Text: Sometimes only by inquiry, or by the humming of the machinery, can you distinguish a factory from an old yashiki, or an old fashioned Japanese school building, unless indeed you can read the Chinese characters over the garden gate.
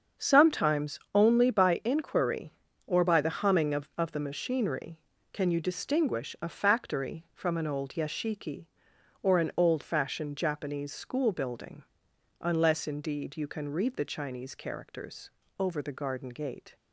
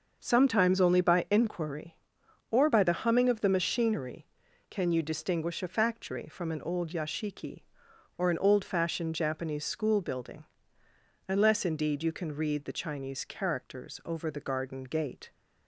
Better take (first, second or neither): second